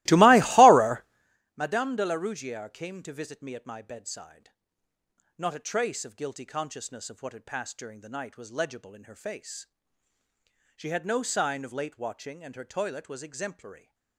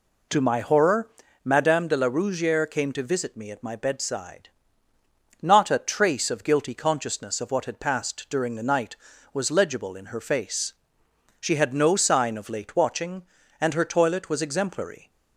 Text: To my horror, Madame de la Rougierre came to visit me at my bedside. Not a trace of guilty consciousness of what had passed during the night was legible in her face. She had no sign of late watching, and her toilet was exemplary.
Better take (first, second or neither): second